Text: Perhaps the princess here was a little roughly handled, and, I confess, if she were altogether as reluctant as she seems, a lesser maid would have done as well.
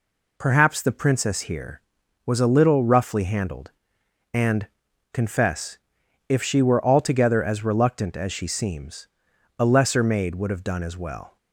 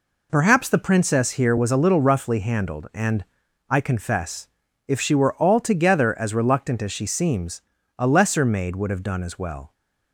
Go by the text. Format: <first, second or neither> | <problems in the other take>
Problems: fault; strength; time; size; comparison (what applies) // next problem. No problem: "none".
second | skips "I"; at 4.9 s